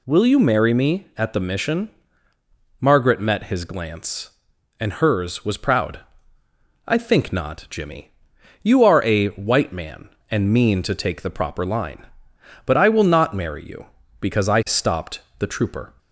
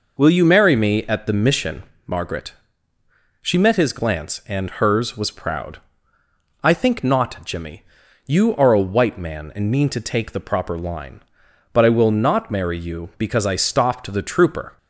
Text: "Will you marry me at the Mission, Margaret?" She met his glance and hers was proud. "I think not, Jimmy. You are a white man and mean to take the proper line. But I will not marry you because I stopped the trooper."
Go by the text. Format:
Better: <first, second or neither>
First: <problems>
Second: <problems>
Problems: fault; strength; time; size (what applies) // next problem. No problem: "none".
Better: second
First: skips "She"; at 3.1 s // pauses between "stopped" and "the"; slight; at 15.2 s; 0.18 s long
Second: none